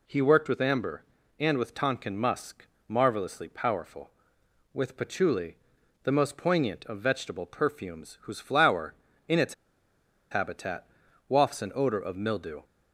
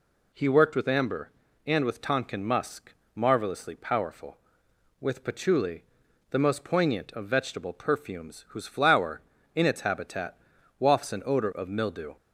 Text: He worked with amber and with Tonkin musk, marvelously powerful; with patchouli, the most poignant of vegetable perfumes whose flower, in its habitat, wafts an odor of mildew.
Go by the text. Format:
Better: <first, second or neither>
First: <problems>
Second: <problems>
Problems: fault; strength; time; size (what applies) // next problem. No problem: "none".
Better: second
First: pauses between "its" and "habitat"; noticeable; at 9.5 s; 0.77 s long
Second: none